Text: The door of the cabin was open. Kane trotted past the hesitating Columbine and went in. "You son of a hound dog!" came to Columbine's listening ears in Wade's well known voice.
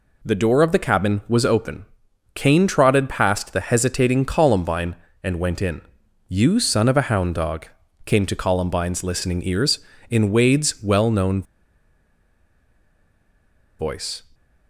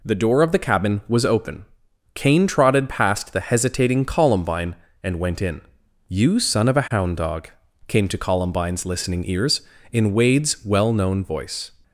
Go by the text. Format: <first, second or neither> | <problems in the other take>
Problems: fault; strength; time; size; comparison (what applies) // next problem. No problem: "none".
second | pauses between "known" and "voice"; strong; at 11.4 s; 2.3 s long